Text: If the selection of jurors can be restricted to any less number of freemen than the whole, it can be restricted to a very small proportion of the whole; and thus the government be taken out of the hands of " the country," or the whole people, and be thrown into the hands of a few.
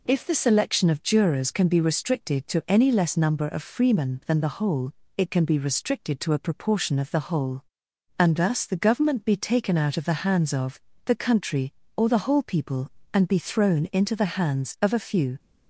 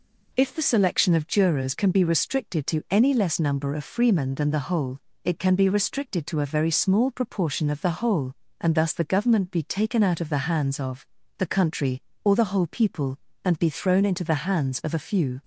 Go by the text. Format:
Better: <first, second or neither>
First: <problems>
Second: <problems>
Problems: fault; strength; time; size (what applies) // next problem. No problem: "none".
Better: second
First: skips "very small"; at 6.3 s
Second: none